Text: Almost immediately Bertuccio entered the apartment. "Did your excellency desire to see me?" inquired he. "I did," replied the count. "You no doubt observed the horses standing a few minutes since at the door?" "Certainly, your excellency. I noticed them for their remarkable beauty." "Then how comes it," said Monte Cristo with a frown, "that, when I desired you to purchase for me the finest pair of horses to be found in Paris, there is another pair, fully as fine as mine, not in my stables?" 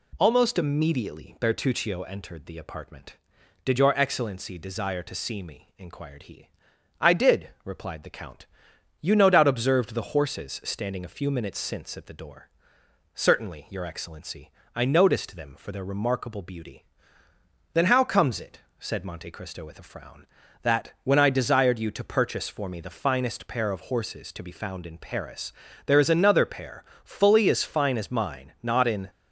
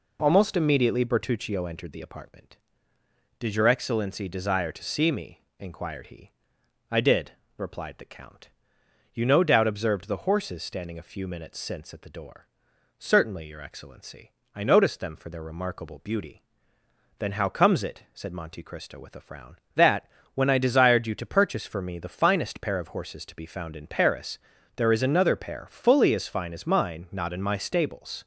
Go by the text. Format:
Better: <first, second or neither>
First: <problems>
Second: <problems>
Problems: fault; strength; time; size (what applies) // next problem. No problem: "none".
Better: second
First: stops before "my stables"; at 29.0 s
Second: none